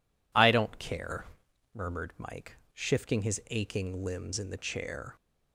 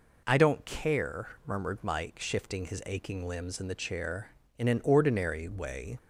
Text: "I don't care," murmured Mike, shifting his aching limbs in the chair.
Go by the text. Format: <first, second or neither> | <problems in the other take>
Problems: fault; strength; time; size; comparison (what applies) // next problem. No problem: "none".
first | goes on to say "In an ordinary way"; from 4.5 s on; 1.4 s long